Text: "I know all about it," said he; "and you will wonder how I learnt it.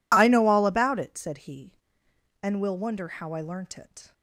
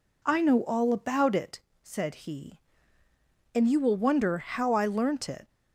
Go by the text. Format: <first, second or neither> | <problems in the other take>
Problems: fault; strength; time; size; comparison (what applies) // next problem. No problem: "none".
second | skips "you"; at 2.6 s